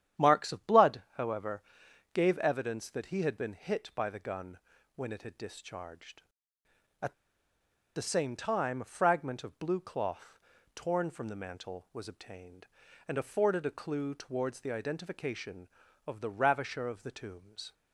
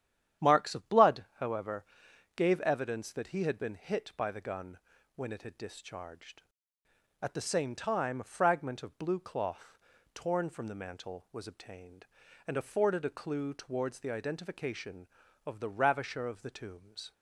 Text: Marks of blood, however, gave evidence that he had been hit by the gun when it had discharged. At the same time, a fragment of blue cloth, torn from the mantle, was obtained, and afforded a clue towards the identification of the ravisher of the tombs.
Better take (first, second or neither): second